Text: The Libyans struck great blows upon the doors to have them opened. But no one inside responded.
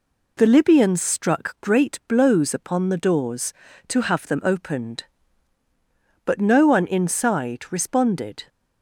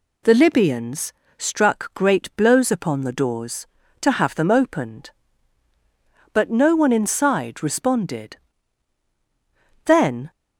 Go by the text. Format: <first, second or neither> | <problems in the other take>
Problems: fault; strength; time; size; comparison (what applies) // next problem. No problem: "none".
first | pauses between "Libyans" and "struck"; slight; at 1.1 s; 0.24 s long // goes on to say "Then"; slight; from 9.8 s on; 0.46 s long